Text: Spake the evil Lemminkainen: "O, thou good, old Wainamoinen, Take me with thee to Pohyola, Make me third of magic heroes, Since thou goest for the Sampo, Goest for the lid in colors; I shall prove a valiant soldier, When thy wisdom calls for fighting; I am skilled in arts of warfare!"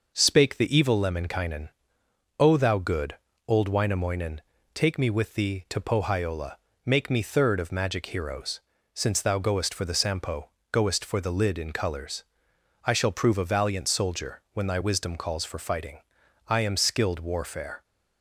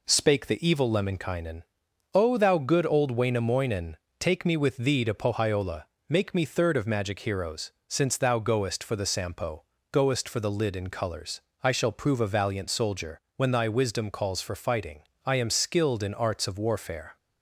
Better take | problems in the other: second | skips "in arts of"; at 17.1 s

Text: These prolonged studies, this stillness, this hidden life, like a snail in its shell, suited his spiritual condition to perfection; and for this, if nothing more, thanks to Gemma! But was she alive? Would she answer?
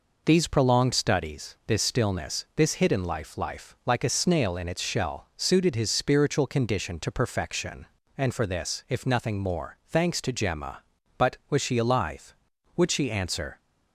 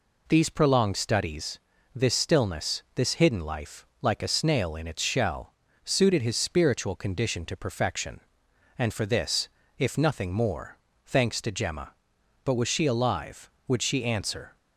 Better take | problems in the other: second | says "life" twice; at 3.3 s

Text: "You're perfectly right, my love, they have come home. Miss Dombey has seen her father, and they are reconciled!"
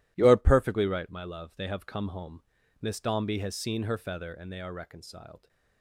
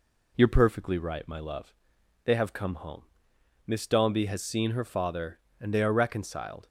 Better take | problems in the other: second | says "feather" for "father"; at 3.9 s

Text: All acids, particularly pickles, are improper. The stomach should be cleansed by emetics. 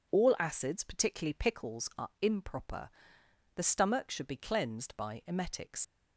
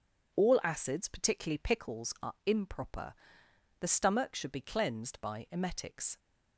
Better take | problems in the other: second | leaves "emetics" unfinished; at 5.8 s; 95 ms

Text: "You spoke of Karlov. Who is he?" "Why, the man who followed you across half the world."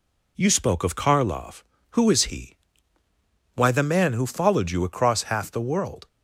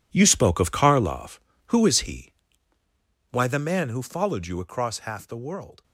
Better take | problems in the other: first | gets quieter; strong; throughout; 13.5 dB

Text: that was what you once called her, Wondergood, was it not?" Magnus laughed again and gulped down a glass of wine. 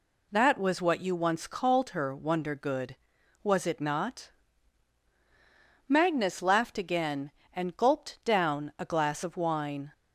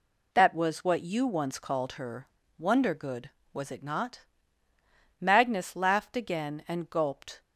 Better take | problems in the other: first | stops before "down a glass of wine"; at 7.4 s

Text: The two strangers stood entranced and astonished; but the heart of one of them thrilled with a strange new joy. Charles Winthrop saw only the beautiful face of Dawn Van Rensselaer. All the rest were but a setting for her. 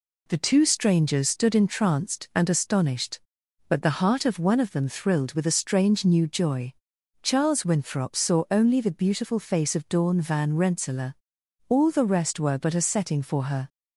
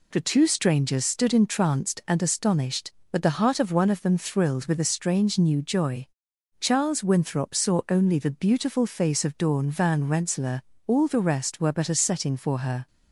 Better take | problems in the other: neither | none

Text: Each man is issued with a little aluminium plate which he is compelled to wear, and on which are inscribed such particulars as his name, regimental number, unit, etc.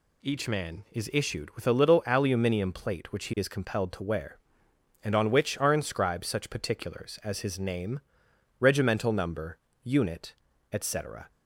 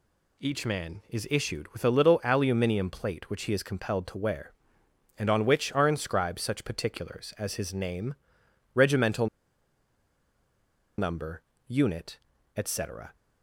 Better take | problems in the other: first | pauses between "regimental" and "number"; strong; at 9.2 s; 1.7 s long

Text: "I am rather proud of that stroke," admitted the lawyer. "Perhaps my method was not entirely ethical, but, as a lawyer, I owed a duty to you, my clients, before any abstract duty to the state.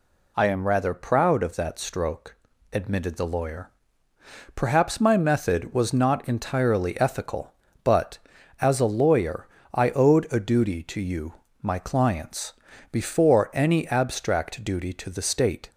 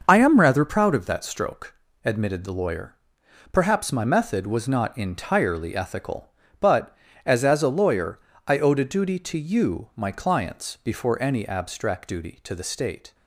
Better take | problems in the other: first | starts louder than the rest; until 1.0 s; 6 dB // says "as" twice; at 7.4 s

